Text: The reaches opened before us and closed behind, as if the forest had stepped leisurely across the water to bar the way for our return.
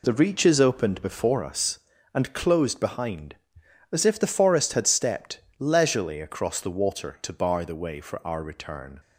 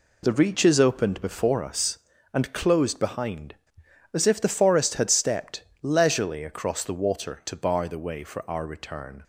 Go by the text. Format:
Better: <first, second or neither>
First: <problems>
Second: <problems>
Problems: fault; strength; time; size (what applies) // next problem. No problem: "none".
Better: neither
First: pauses between "stepped" and "leisurely"; slight; at 5.3 s; 0.20 s long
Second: pauses between "stepped" and "leisurely"; slight; at 5.6 s; 0.20 s long